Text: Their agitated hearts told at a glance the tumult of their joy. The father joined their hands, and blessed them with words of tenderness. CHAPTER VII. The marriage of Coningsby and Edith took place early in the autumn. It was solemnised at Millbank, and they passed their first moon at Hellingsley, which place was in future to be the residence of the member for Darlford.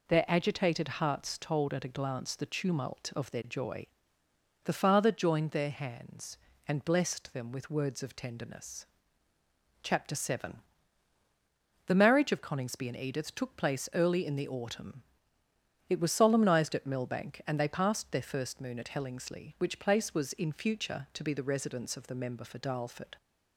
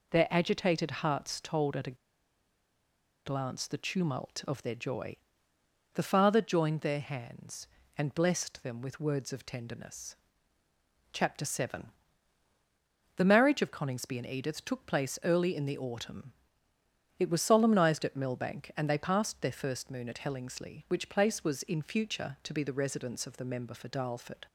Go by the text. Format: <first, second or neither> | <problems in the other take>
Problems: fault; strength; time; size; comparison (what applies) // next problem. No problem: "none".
first | pauses between "a" and "glance"; strong; at 1.9 s; 1.3 s long